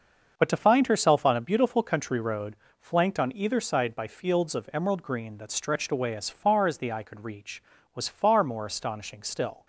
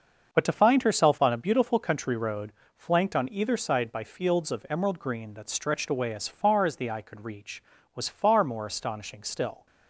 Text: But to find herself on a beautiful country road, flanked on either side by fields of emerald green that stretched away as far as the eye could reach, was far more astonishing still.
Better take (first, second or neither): neither